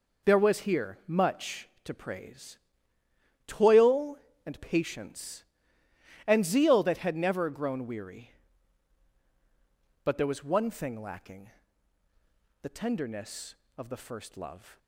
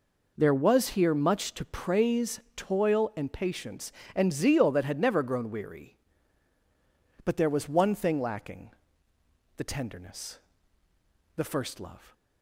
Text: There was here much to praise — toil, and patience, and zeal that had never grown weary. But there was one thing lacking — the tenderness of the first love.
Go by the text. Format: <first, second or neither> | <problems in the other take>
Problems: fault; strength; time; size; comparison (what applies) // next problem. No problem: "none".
first | skips "of"; at 10.8 s